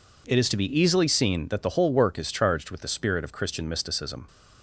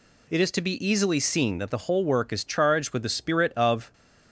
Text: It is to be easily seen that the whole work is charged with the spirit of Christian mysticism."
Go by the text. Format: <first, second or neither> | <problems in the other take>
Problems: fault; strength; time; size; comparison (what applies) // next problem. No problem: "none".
first | stops before "Christian mysticism"; at 3.9 s